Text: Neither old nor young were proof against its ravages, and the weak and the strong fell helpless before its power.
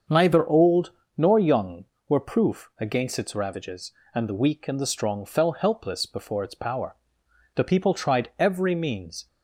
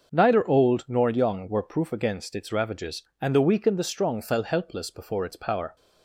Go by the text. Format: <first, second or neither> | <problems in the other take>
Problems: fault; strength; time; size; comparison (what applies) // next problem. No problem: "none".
second | starts louder than the rest; until 1.3 s; 6.5 dB // pauses between "old" and "nor"; slight; at 0.9 s; 0.26 s long // goes on to say "The people tried every means"; strong; from 7.5 s on; 1.7 s long